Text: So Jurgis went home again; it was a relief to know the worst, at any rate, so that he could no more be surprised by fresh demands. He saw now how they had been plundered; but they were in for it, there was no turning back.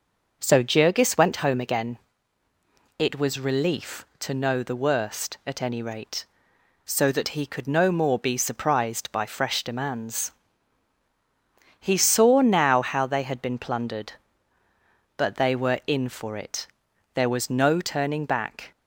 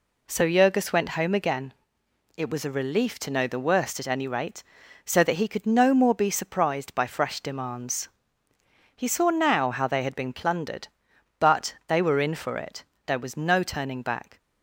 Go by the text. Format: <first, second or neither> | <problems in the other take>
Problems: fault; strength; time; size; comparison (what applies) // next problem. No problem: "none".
second | skips "a"; at 3.4 s